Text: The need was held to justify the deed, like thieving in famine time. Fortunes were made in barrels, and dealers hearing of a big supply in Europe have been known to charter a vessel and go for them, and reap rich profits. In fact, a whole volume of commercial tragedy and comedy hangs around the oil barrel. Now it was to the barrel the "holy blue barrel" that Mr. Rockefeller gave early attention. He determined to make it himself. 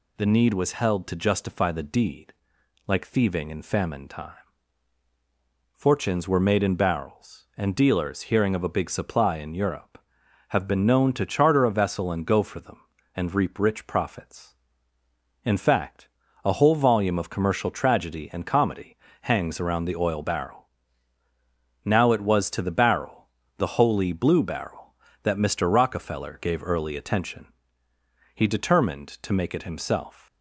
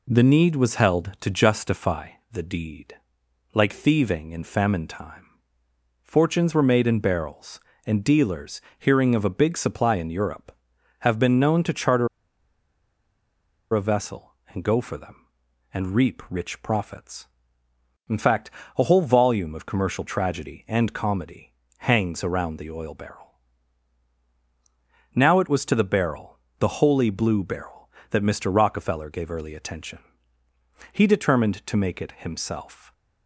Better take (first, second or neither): first